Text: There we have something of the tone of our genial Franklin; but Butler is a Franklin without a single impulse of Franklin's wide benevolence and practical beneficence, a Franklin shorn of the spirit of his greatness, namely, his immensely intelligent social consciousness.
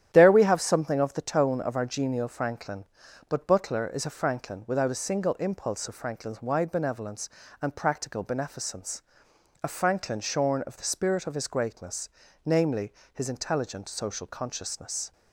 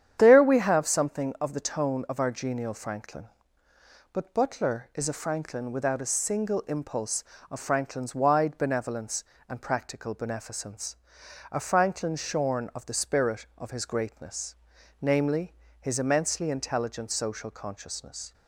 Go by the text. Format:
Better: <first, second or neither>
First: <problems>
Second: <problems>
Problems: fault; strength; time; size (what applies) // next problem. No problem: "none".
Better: second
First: starts louder than the rest; strong; until 1.1 s; 10.5 dB // skips "immensely"; at 13.2 s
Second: starts louder than the rest; strong; until 1.2 s; 9 dB